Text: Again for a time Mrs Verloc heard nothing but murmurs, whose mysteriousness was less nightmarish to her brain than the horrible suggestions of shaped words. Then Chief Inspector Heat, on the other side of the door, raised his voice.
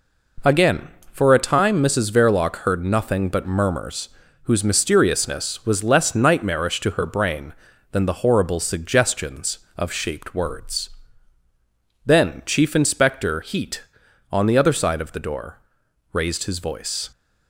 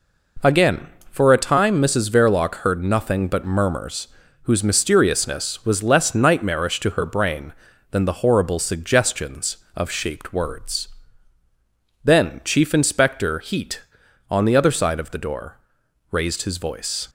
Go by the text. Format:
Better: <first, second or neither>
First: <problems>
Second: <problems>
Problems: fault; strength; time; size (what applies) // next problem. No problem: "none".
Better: neither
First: none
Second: none